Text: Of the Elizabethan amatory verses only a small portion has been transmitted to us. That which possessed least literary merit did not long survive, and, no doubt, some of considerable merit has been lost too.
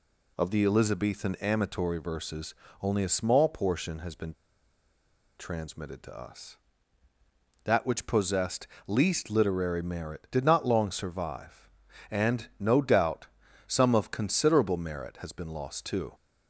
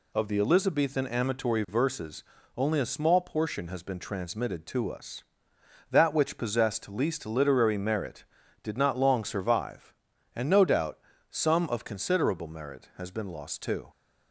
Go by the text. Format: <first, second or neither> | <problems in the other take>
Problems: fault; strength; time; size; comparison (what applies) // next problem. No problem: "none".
second | pauses between "verses" and "only"; slight; at 2.5 s; 0.26 s long; slight in the second // pauses between "been" and "transmitted"; at 4.3 s; 1.0 s long // pauses between "possessed" and "least"; slight; at 8.6 s; 0.22 s long